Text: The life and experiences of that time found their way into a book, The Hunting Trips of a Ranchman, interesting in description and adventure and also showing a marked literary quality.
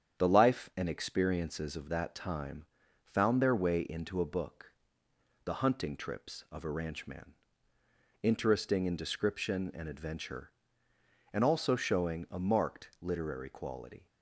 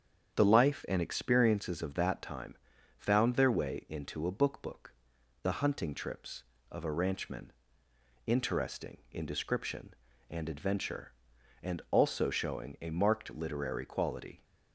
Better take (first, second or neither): first